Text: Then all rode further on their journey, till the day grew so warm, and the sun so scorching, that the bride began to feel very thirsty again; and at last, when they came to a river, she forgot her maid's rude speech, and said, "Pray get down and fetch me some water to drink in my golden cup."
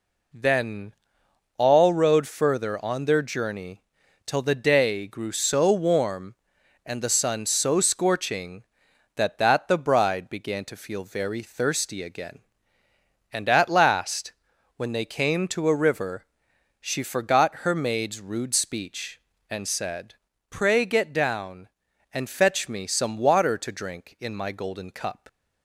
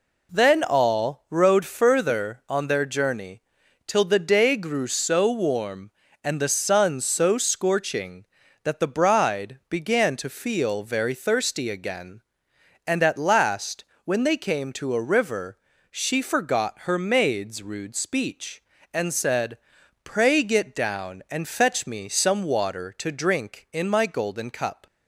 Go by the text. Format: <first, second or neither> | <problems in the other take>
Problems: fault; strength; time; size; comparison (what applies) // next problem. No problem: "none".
second | pauses between "Then" and "all"; noticeable; at 0.9 s; 0.64 s long // says "that" twice; at 9.3 s